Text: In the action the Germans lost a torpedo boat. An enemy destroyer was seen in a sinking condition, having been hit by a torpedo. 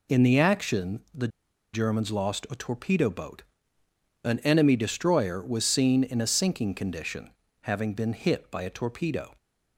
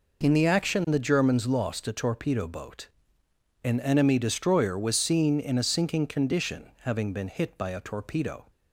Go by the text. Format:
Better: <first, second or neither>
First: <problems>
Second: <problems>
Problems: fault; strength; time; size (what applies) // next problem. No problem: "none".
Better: second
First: pauses between "the" and "Germans"; at 1.2 s; 0.45 s long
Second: none